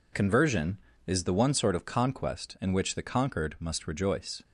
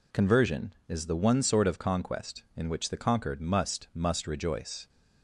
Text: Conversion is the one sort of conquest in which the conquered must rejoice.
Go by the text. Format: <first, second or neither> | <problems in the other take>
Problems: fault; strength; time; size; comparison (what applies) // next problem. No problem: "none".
first | says "must" twice; at 3.9 s